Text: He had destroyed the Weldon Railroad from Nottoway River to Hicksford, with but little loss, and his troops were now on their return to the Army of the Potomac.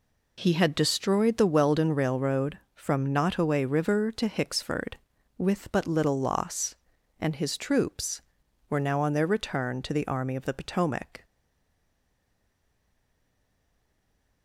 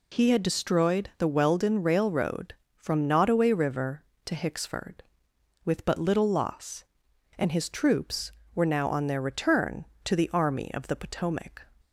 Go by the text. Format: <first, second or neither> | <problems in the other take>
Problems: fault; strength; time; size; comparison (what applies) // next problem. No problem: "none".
second | stays silent after the last word; strong; from 11.2 s on; 3.2 s long